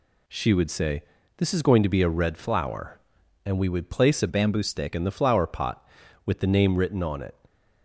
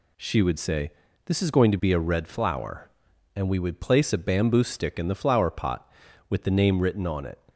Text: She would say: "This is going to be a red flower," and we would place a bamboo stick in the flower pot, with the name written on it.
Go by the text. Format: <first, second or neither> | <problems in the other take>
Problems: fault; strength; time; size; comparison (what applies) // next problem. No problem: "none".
second | changes voice from "bamboo" to "stick"; from 4.2 to 4.9 s; 0.7 s long